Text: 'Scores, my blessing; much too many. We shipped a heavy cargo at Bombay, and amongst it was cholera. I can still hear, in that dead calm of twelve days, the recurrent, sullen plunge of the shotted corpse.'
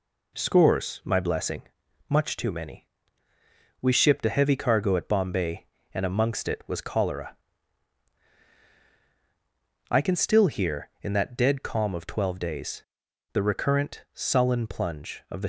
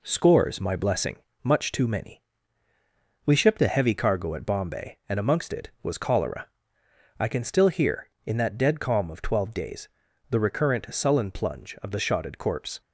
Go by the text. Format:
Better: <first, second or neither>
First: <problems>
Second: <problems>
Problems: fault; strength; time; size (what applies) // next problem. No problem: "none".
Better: second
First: stops before "shotted corpse"; at 15.4 s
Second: none